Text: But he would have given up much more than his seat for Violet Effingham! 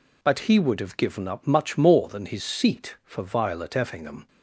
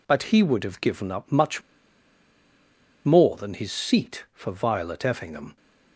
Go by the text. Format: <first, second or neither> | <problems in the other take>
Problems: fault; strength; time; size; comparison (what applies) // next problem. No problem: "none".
first | pauses between "much" and "more"; strong; at 1.6 s; 1.4 s long